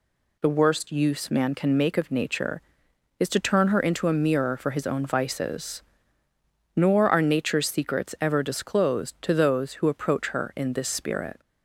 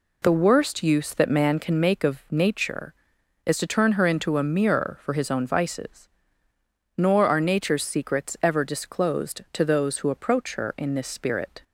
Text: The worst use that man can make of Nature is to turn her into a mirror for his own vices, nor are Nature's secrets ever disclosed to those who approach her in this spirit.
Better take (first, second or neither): second